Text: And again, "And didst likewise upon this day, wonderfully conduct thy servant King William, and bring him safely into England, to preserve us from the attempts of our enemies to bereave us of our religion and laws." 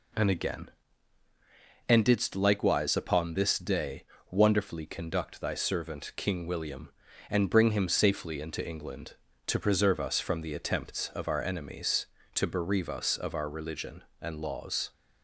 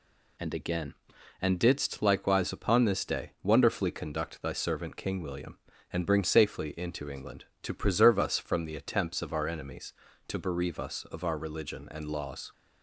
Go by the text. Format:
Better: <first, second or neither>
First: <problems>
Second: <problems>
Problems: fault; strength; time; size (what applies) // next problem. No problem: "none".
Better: first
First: none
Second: skips "him"; at 6.2 s